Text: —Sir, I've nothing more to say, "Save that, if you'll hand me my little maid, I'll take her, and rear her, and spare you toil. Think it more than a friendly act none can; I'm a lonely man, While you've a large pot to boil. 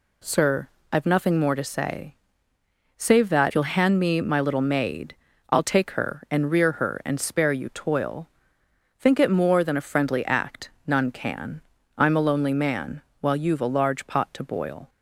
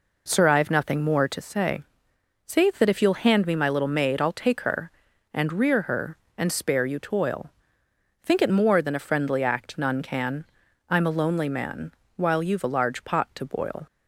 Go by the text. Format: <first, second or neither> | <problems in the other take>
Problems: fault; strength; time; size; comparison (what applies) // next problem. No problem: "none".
second | skips "if"; at 3.5 s // pauses between "act" and "none"; slight; at 10.7 s; 0.16 s long